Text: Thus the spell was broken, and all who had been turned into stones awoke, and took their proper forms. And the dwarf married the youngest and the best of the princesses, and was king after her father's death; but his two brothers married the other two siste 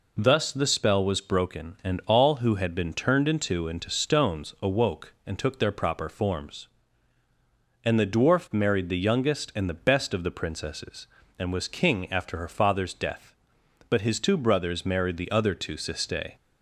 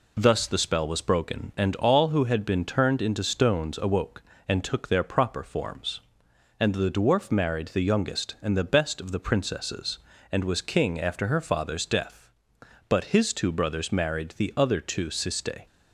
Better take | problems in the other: second | says "into" twice; at 3.6 s

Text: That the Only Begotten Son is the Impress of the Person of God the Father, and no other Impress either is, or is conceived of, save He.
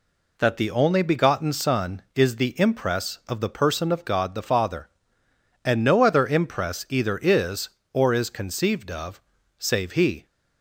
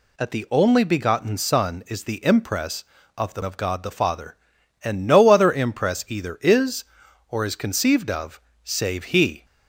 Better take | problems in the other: first | skips "Person"; at 3.4 s

